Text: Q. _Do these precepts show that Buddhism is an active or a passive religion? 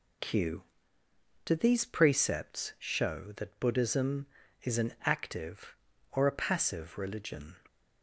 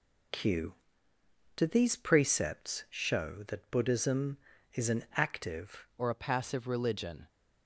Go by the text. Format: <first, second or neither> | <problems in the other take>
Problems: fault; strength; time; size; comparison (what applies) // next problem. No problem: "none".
first | changes voice at "or"; from 5.9 s on; 1.3 s long